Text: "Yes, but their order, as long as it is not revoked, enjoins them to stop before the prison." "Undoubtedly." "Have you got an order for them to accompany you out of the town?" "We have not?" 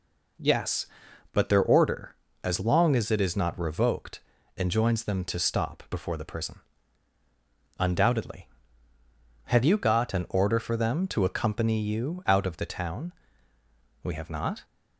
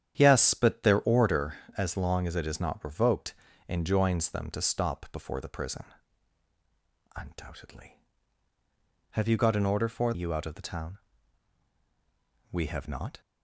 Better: first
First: none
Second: starts louder than the rest; strong; until 1.1 s; 9 dB // skips "them to accompany"; at 10.1 s

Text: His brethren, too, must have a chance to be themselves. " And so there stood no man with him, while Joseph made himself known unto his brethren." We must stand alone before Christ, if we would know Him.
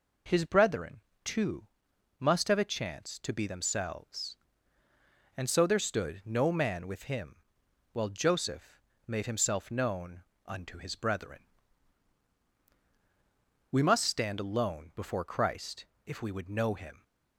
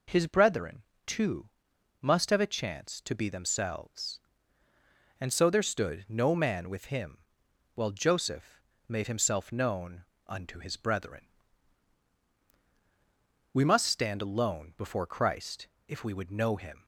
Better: neither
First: pauses between "Joseph" and "made"; slight; at 8.7 s; 0.26 s long // pauses between "known" and "unto"; slight; at 10.2 s; 0.24 s long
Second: pauses between "Joseph" and "made"; slight; at 8.6 s; 0.26 s long // pauses between "known" and "unto"; slight; at 10.0 s; 0.24 s long

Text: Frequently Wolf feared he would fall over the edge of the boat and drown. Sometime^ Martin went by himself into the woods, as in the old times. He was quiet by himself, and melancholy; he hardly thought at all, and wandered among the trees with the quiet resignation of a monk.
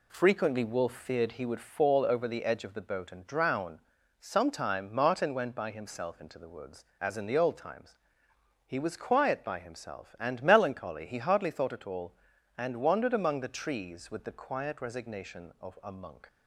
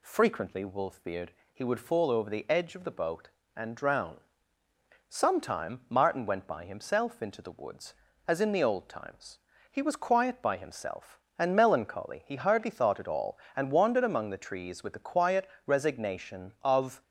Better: first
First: none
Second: pauses between "feared" and "he"; slight; at 1.3 s; 0.20 s long // pauses between "quiet" and "resignation"; slight; at 15.4 s; 0.18 s long // stops before "a monk"; at 17.0 s

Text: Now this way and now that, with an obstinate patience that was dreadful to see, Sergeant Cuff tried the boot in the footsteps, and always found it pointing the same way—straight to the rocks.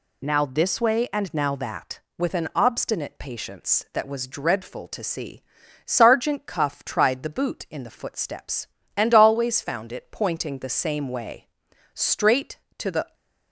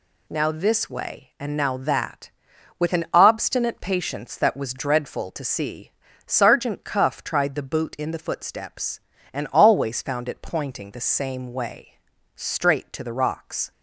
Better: second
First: stops before "rocks"; at 13.1 s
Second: none

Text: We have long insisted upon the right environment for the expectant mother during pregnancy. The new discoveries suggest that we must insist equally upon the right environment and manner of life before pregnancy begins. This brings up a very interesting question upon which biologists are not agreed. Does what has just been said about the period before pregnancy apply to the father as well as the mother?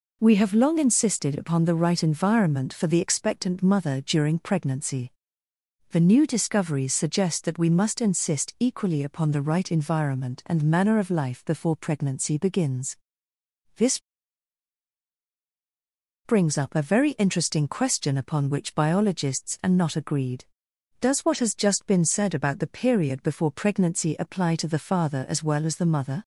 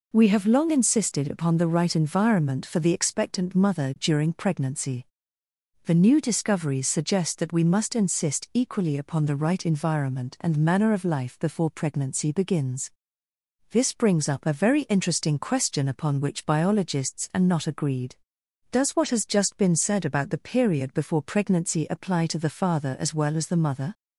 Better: second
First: pauses between "This" and "brings"; strong; at 13.9 s; 2.2 s long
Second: none

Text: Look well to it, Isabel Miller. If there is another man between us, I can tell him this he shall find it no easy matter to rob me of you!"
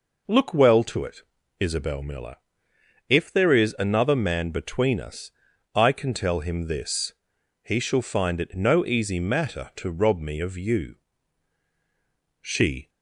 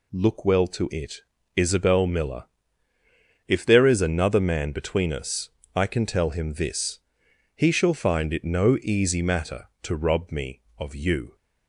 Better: second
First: pauses between "this" and "he"; noticeable; at 7.1 s; 0.52 s long // goes on to say "She"; slight; from 12.4 s on; 0.48 s long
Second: pauses between "this" and "he"; noticeable; at 6.9 s; 0.56 s long

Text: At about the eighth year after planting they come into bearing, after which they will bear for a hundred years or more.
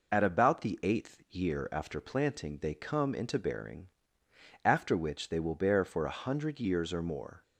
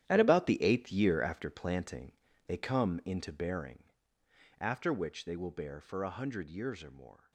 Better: first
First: none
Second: gets quieter; strong; throughout; 13 dB // pauses between "planting" and "they"; slight; at 2.1 s; 0.34 s long

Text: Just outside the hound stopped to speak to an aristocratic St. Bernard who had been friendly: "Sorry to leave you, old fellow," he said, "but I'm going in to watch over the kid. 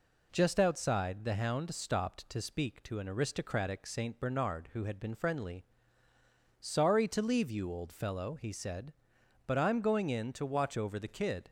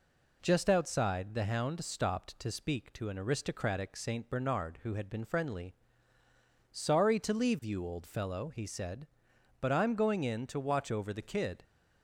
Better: neither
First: none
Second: none

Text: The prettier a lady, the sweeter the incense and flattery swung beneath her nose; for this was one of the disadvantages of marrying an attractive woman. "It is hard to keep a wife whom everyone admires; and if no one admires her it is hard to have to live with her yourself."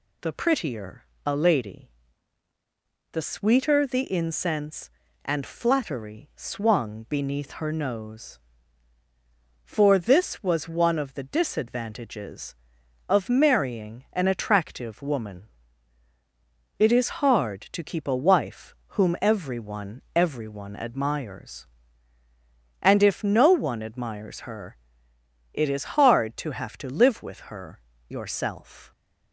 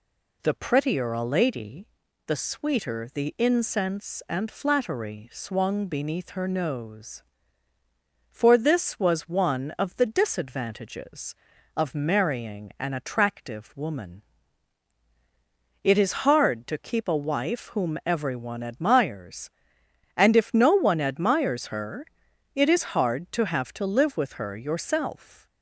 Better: second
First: pauses between "prettier" and "a"; slight; at 1.0 s; 0.20 s long // pauses between "wife" and "whom"; slight; at 18.7 s; 0.24 s long // says "everyone" twice; at 20.1 s // pauses between "her" and "it"; noticeable; at 24.7 s; 0.78 s long // pauses between "her" and "yourself"; slight; at 27.7 s; 0.30 s long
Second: pauses between "her" and "it"; noticeable; at 22.0 s; 0.48 s long

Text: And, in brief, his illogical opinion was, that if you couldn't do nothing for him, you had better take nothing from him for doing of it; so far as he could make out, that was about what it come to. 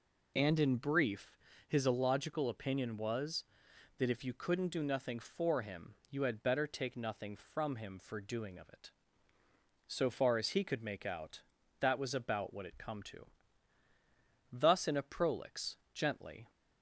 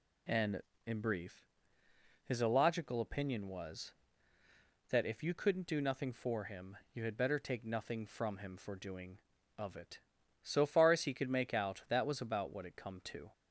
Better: second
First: goes on to say "Thus in a prolix gently"; strong; from 14.4 s on; 2.0 s long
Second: none

